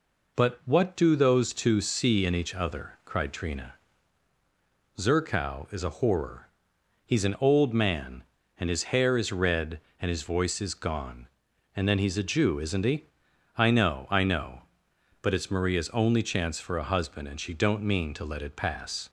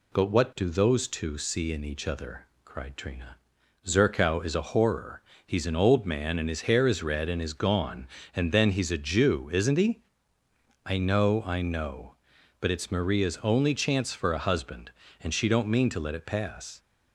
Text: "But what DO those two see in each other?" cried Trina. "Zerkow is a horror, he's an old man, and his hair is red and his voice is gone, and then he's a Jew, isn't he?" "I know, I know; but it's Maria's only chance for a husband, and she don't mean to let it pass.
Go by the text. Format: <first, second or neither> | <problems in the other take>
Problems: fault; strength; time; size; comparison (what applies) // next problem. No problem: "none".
first | skips "his voice"; at 7.4 s